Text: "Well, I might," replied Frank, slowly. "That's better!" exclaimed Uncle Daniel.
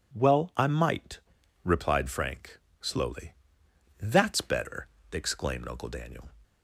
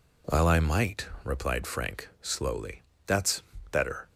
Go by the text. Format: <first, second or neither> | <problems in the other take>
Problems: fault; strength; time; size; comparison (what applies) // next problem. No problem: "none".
first | pauses between "That's" and "better"; slight; at 3.4 s; 0.28 s long // stops before "exclaimed Uncle Daniel"; at 4.0 s